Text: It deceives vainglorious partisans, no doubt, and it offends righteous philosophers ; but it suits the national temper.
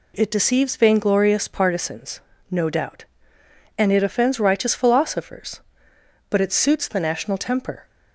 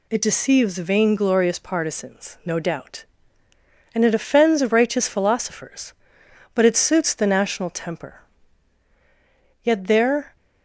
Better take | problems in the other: first | goes on to say "Yet there"; noticeable; from 9.6 s on; 0.72 s long

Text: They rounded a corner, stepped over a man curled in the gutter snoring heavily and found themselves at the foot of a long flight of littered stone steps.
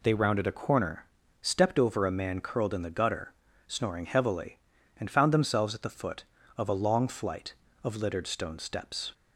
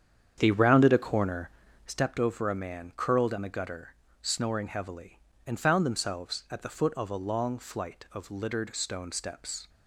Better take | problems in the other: first | starts louder than the rest; strong; until 2.1 s; 8.5 dB // pauses between "gutter" and "snoring"; slight; at 3.9 s; 0.26 s long; slight in the first

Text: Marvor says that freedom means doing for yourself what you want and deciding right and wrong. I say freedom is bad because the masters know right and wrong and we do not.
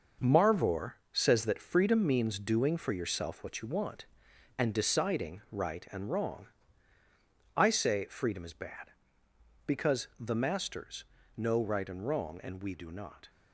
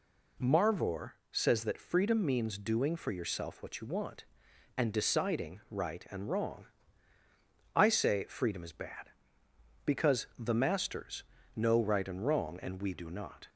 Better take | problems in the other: second | gets quieter; strong; throughout; 8.5 dB // pauses between "Marvor" and "says"; slight; at 0.9 s; 0.20 s long; slight in the second // pauses between "masters" and "know"; slight; at 11.0 s; 0.32 s long; slight in the second

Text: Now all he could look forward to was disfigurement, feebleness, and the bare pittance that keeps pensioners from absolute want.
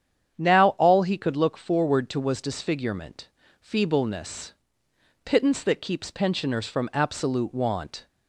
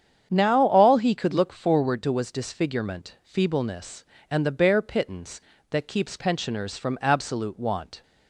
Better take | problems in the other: second | starts louder than the rest; strong; until 1.3 s; 8.5 dB; strong in the second // skips "and the bare"; at 4.8 s

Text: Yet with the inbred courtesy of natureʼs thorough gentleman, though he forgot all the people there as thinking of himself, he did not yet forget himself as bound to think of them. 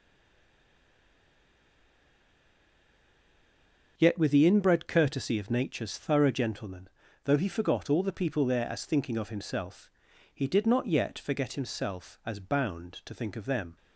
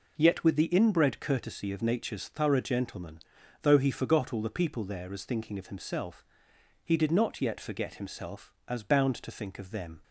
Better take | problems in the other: second | stays silent before the first word; strong; until 3.9 s; 3.9 s long

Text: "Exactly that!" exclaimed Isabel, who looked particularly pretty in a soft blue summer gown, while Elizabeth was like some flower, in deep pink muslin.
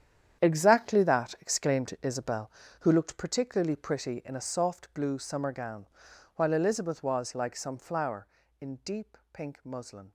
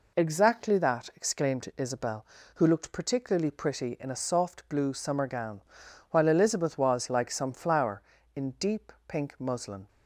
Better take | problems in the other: second | gets quieter; strong; throughout; 13 dB // pauses between "deep" and "pink"; slight; at 9.1 s; 0.16 s long; slight in the second

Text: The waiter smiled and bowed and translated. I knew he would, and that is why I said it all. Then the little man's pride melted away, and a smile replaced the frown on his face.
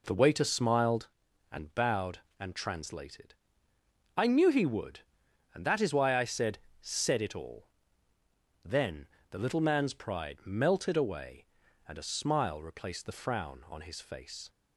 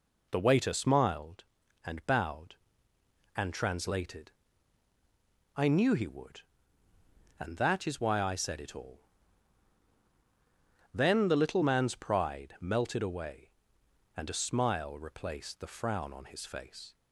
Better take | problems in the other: second | says "said" twice; at 6.7 s // pauses between "Then" and "the"; slight; at 9.0 s; 0.24 s long

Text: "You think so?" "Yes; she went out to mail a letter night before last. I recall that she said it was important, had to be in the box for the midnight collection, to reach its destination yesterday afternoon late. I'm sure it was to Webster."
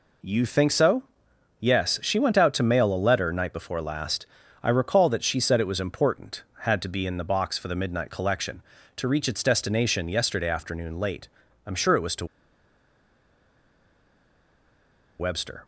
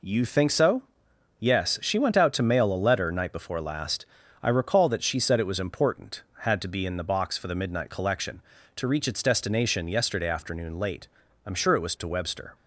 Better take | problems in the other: second | pauses between "to" and "Webster"; strong; at 12.2 s; 2.9 s long

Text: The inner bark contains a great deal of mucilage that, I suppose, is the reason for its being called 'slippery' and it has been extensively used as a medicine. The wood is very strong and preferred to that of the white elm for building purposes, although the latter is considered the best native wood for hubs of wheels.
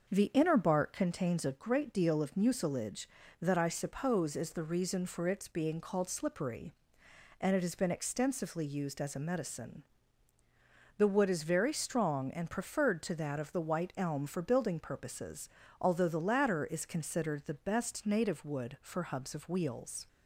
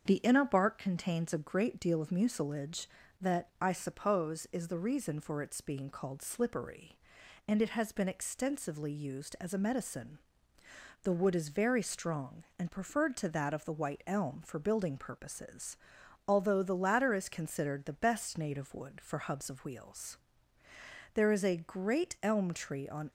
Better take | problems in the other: first | starts louder than the rest; until 1.0 s; 7 dB; noticeable in the first // goes on to say "There is a great elm tree on"; strong; from 21.1 s on; 1.9 s long

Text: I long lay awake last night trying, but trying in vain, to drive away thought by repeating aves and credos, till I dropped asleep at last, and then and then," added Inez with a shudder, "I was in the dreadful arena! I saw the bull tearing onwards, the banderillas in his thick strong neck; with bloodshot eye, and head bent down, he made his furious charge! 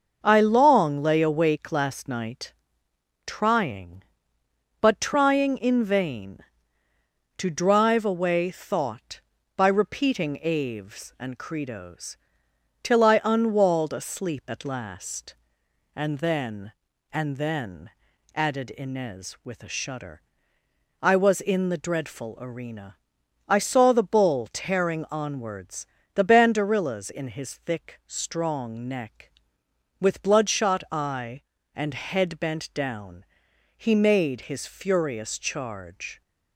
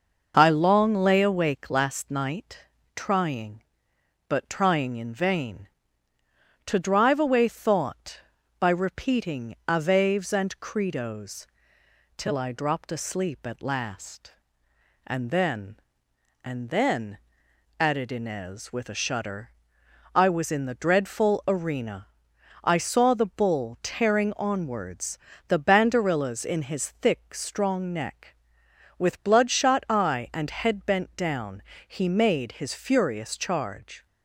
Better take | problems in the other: second | starts louder than the rest; until 1.2 s; 6 dB // pauses between "night" and "trying"; noticeable; at 2.5 s; 0.74 s long; slight in the second // says "unwalled" for "dropped"; at 13.2 s

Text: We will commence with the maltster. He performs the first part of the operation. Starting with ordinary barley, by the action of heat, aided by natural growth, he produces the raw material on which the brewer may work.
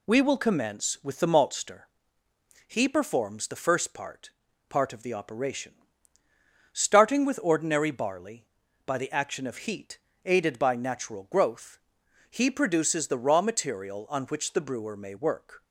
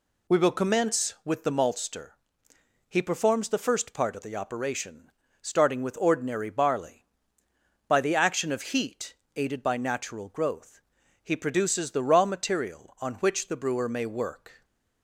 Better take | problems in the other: second | says "part" twice; at 4.6 s

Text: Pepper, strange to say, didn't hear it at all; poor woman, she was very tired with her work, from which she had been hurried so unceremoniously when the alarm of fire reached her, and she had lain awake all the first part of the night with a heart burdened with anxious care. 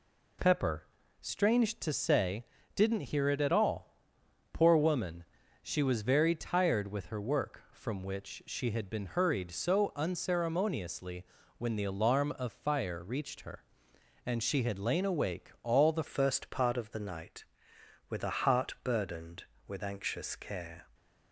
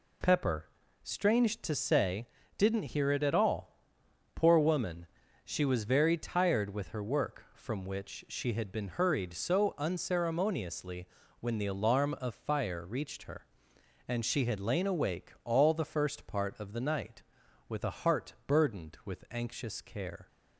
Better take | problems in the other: second | pauses between "unceremoniously" and "when"; slight; at 11.2 s; 0.32 s long; slight in the second // changes voice at "first"; from 16.0 s on; 4.8 s long

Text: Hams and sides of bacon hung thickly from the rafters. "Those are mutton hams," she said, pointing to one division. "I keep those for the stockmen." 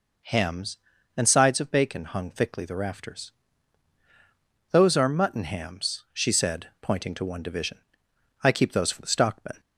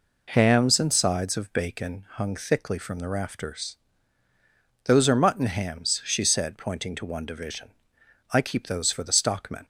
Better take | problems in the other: second | skips "from"; at 2.6 s

